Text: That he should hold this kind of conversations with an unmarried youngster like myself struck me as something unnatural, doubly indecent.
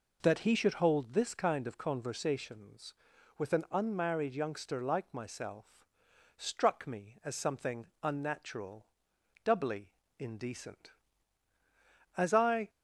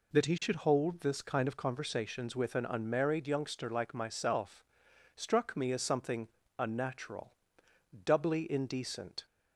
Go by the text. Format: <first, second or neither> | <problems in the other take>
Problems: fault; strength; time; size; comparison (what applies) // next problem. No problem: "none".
second | pauses between "myself" and "struck"; noticeable; at 5.6 s; 0.70 s long; noticeable in the second // pauses between "something" and "unnatural"; slight; at 7.8 s; 0.18 s long; slight in the second // pauses between "doubly" and "indecent"; slight; at 9.9 s; 0.26 s long // goes on to say "As I"; from 12.1 s on; 0.52 s long